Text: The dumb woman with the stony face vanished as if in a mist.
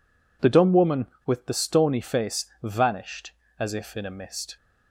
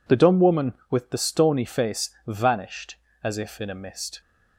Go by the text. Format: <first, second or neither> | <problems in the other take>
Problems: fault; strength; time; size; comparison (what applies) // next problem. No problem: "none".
neither | pauses between "face" and "vanished"; slight; the same in both